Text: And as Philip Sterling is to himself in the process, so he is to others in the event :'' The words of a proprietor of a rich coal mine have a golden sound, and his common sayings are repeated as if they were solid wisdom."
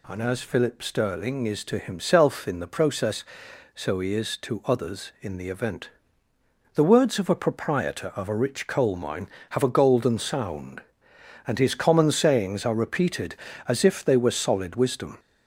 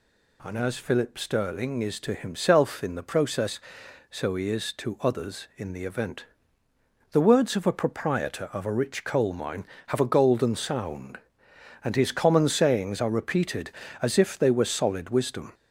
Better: neither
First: none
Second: none

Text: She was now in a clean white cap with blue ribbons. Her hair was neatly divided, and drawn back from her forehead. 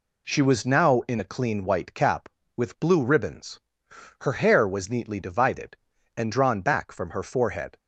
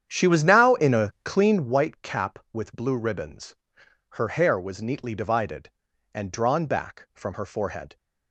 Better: first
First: none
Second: starts louder than the rest; strong; until 1.8 s; 9 dB

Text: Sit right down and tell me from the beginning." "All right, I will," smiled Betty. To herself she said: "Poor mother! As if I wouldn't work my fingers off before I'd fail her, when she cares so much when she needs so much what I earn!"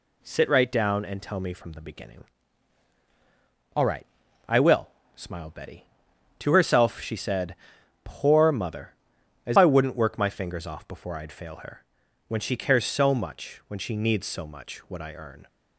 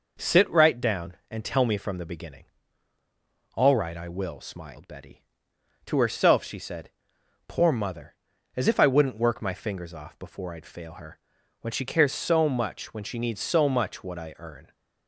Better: second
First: skips "if"; at 9.5 s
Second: none

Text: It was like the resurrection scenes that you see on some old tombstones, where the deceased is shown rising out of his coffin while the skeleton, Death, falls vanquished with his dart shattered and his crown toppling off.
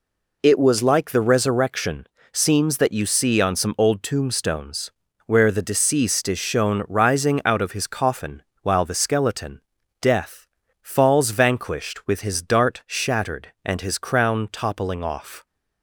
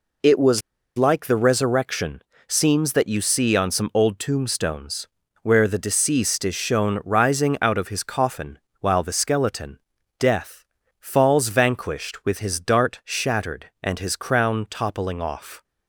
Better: first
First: pauses between "resurrection" and "scenes"; slight; at 2.0 s; 0.26 s long // pauses between "coffin" and "while"; slight; at 8.4 s; 0.18 s long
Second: pauses between "was" and "like"; at 0.6 s; 0.38 s long // pauses between "resurrection" and "scenes"; slight; at 2.2 s; 0.26 s long // pauses between "coffin" and "while"; slight; at 8.5 s; 0.20 s long

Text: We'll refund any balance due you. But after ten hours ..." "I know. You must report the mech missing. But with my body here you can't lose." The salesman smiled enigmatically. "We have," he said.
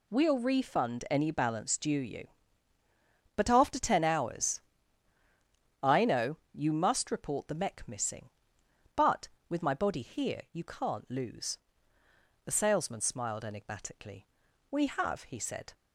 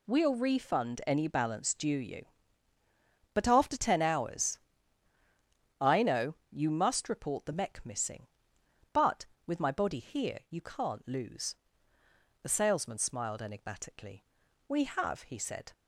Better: neither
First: none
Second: none

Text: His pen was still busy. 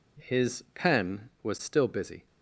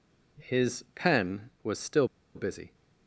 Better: first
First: none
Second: pauses between "still" and "busy"; slight; at 2.0 s; 0.29 s long

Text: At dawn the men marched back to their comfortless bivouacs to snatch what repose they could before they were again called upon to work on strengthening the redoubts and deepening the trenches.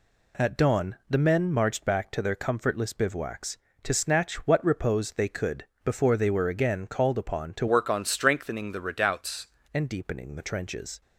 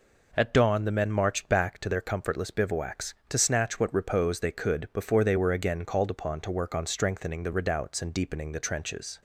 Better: second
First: pauses between "could" and "before"; slight; at 5.6 s; 0.22 s long // changes voice from "work" to "redoubts"; from 7.6 to 9.4 s; 1.8 s long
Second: none

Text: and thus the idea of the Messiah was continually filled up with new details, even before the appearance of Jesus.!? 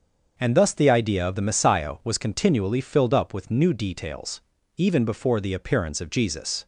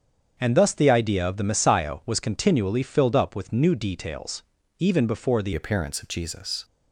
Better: first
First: starts louder than the rest; until 1.3 s; 6.5 dB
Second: starts louder than the rest; strong; until 1.4 s; 7.5 dB // changes voice at "appearance"; from 5.5 s on; 1.1 s long

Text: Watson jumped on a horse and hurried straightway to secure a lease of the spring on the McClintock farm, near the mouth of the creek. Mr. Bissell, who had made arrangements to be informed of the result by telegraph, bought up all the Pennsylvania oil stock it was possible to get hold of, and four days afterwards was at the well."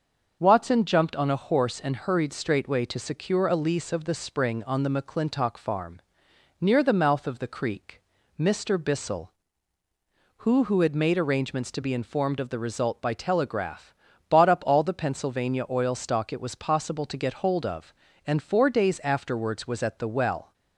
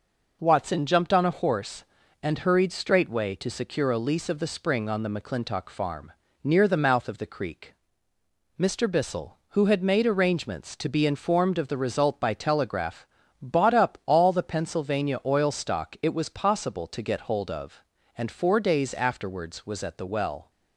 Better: second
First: starts louder than the rest; until 1.4 s; 6.5 dB // says "who" twice; at 10.6 s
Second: none

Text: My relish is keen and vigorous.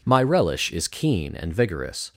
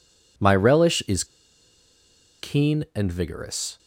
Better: first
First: none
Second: pauses between "is" and "keen"; at 1.2 s; 1.1 s long

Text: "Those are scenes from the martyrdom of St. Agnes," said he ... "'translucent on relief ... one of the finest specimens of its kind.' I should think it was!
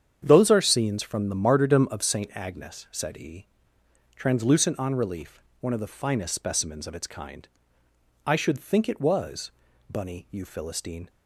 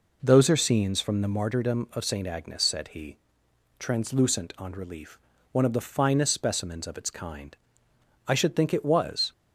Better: second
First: starts louder than the rest; strong; until 1.2 s; 8 dB // goes on to say "Bunny you Philistine"; noticeable; from 9.8 s on; 1.2 s long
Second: none

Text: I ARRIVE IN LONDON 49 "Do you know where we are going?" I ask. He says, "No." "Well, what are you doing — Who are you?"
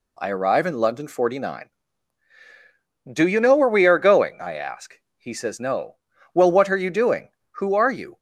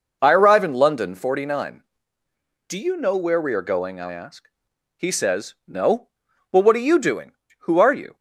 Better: neither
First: none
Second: none

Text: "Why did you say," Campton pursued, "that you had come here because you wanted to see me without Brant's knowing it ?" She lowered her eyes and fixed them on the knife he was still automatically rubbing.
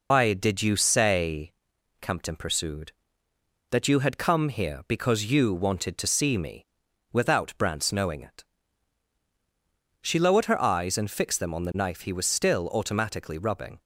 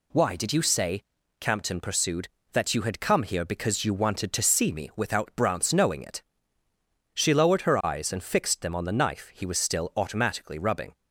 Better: second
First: loses the start of "Why"; at 0.1 s; 125 ms // pauses between "me" and "without"; noticeable; at 6.6 s; 0.46 s long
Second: none

